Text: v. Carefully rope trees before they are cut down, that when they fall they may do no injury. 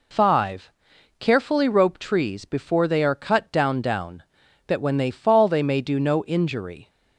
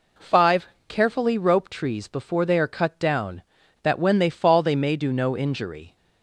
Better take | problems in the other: second | says "down" twice; at 3.7 s

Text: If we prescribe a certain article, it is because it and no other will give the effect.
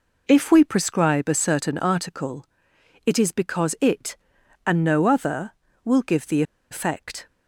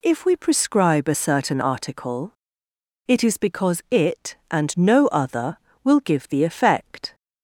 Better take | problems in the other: second | pauses between "the" and "effect"; slight; at 6.4 s; 0.28 s long

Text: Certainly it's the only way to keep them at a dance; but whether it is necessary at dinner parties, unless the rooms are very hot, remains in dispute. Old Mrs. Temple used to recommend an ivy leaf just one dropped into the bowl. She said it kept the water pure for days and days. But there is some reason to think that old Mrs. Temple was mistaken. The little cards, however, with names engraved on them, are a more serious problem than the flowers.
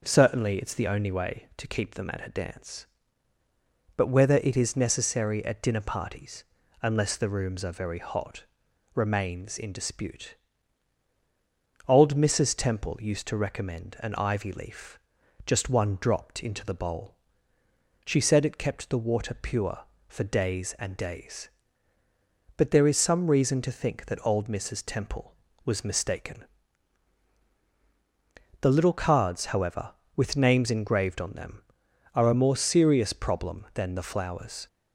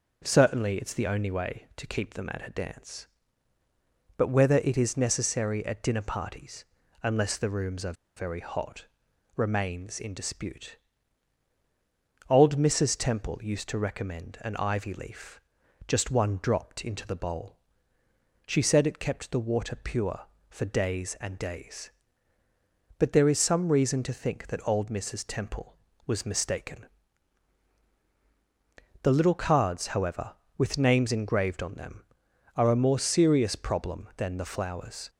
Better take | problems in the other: first | pauses between "are" and "very"; slight; at 7.9 s; 0.23 s long // pauses between "leaf" and "just"; noticeable; at 15.3 s; 0.46 s long; noticeable in the first

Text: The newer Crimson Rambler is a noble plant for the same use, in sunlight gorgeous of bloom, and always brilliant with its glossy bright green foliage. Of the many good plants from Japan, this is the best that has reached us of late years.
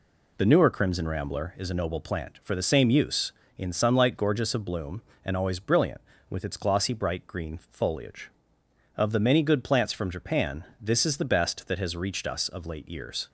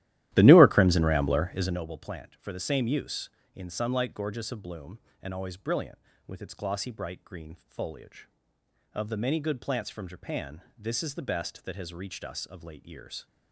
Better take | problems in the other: first | starts louder than the rest; strong; until 1.8 s; 14 dB

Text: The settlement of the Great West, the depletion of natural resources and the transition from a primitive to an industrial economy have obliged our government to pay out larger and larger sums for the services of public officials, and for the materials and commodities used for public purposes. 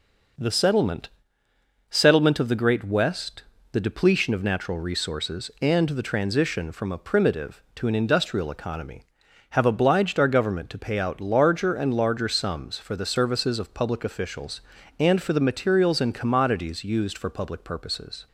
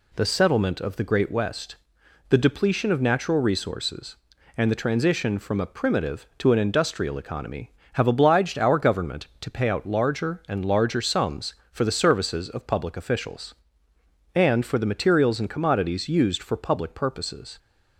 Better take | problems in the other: second | says "settlement" twice; at 1.8 s

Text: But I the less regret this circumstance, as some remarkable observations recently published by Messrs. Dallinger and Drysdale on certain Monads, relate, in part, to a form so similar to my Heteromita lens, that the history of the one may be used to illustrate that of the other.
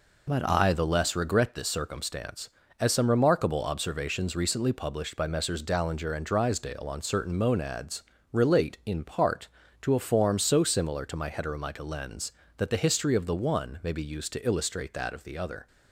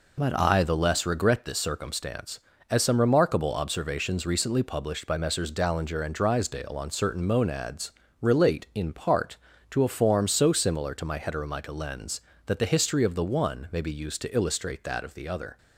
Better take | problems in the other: neither | none

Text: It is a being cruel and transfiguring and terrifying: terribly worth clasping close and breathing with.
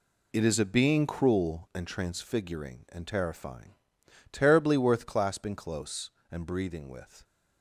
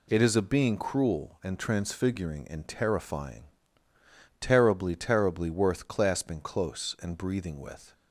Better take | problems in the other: first | says "terribly" twice; at 4.9 s

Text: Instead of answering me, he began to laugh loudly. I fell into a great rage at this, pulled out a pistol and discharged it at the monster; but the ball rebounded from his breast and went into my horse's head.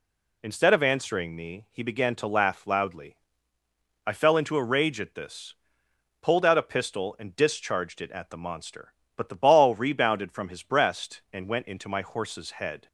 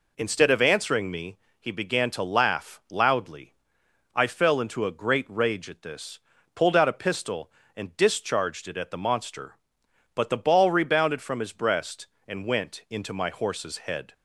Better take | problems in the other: second | skips "great"; at 4.6 s

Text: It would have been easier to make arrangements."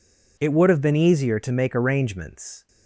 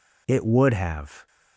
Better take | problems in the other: first | stops before "been easier to make arrangements"; at 1.2 s

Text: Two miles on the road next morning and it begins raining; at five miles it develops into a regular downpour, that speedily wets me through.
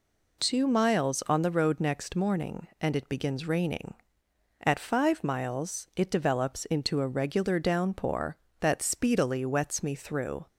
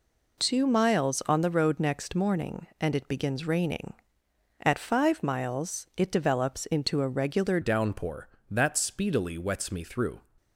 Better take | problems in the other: first | changes voice at "downpour"; from 7.6 s on; 2.6 s long

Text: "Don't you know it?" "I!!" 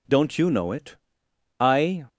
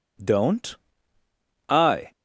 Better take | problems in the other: first | skips "you know it"; at 1.2 s

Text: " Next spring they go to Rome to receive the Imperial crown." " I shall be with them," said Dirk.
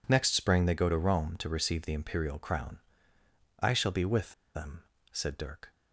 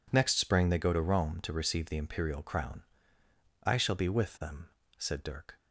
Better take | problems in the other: second | pauses between "with" and "them"; slight; at 4.3 s; 0.21 s long

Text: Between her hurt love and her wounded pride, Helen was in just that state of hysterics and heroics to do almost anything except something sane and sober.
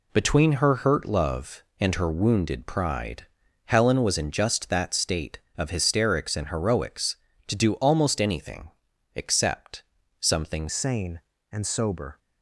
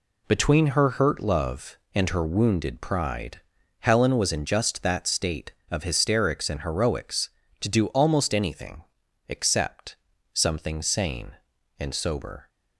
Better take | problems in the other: second | pauses between "anything" and "except"; at 8.6 s; 0.44 s long; also in the second // pauses between "except" and "something"; slight; at 9.8 s; 0.36 s long; slight in the second // changes voice at "sane"; from 10.6 s on; 1.5 s long

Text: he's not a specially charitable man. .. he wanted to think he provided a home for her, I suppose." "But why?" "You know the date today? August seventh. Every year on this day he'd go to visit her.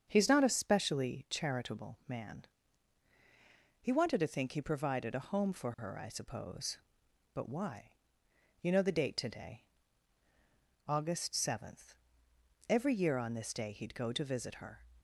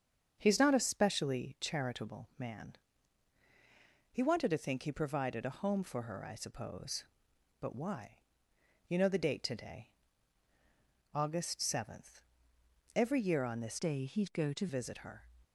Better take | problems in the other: first | starts louder than the rest; until 1.4 s; 7 dB; also in the first // changes voice from "day" to "to"; from 13.7 to 14.6 s; 0.9 s long

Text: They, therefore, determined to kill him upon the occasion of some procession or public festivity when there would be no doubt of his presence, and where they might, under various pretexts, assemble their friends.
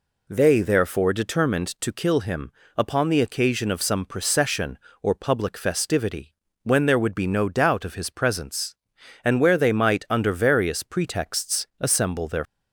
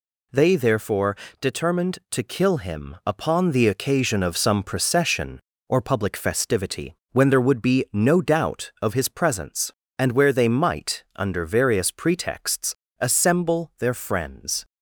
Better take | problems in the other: second | pauses between "him" and "upon"; slight; at 2.5 s; 0.24 s long // pauses between "festivity" and "when"; slight; at 6.3 s; 0.30 s long; slight in the second // stops before "friends"; at 12.4 s

